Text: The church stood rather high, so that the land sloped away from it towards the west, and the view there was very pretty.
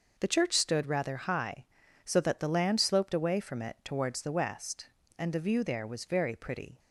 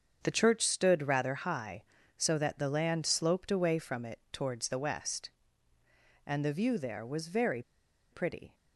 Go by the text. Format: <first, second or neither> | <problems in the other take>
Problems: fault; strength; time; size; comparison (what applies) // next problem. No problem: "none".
first | starts louder than the rest; strong; until 1.2 s; 7 dB // pauses between "very" and "pretty"; noticeable; at 7.6 s; 0.49 s long